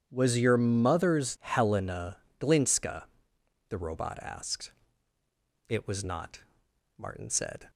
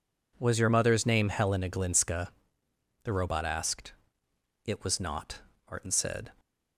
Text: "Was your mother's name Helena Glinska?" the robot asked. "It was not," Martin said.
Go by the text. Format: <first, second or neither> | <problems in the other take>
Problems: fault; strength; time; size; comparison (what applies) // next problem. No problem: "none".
second | starts louder than the rest; strong; until 1.1 s; 9 dB // skips "name"; at 1.3 s // pauses between "Helena" and "Glinska"; slight; at 2.1 s; 0.20 s long